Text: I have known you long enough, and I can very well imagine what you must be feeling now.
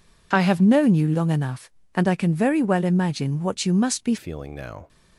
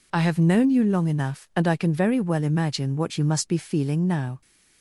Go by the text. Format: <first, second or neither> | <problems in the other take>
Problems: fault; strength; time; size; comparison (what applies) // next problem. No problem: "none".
second | changes voice at "feeling"; from 4.1 s on; 0.7 s long